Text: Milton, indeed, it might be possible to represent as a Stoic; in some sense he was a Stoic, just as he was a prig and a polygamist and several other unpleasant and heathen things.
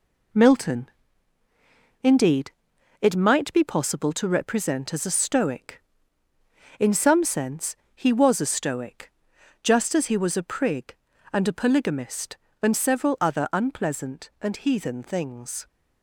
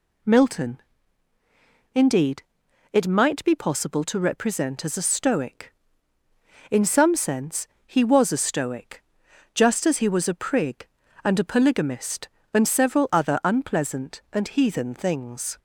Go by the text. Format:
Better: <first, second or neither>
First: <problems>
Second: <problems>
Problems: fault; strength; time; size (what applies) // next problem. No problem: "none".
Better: second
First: gets quieter; noticeable; throughout; 6 dB // pauses between "sense" and "he"; slight; at 7.7 s; 0.20 s long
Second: pauses between "sense" and "he"; slight; at 7.6 s; 0.20 s long